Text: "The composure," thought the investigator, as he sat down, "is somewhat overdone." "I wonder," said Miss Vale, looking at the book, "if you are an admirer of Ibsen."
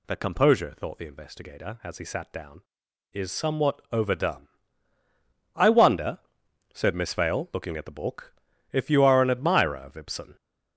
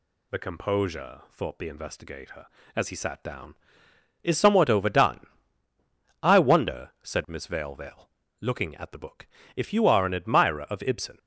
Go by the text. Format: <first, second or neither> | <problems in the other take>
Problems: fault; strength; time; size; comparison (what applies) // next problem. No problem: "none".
first | says "Vale" twice; at 7.7 s